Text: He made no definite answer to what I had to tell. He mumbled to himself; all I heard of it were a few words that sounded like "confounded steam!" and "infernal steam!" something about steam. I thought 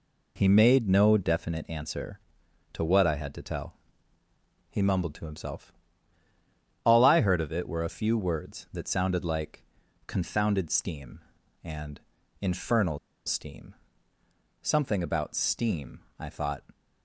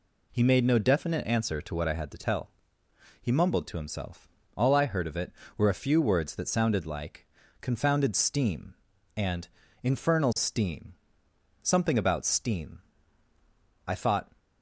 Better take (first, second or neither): second